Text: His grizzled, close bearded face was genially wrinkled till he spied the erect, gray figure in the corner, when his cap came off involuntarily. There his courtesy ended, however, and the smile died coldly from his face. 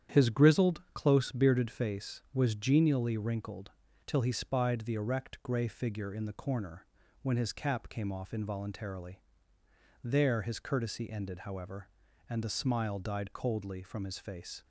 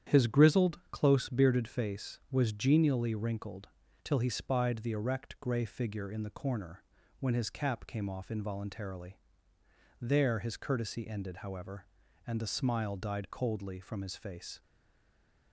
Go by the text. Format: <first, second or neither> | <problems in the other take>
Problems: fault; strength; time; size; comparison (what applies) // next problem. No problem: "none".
first | starts louder than the rest; strong; until 1.1 s; 9.5 dB; strong in the first // pauses between "wrinkled" and "till"; at 3.6 s; 0.38 s long; also in the first // stays silent after the last word; slight; from 14.6 s on; 0.9 s long